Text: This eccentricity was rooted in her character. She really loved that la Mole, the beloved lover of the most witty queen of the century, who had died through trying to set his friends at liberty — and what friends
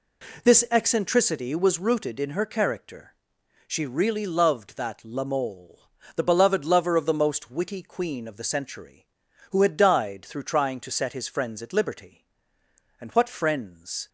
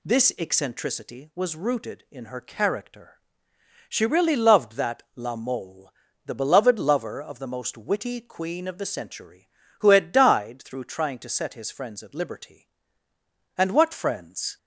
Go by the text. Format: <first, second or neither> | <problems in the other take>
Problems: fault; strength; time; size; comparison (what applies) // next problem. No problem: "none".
neither | none